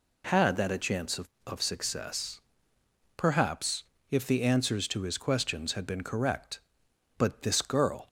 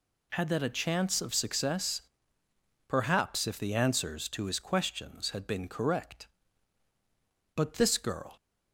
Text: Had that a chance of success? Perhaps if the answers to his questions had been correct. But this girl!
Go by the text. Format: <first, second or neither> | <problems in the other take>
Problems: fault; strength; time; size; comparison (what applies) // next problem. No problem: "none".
second | says "of" twice; at 1.4 s // pauses between "Perhaps" and "if"; slight; at 3.8 s; 0.26 s long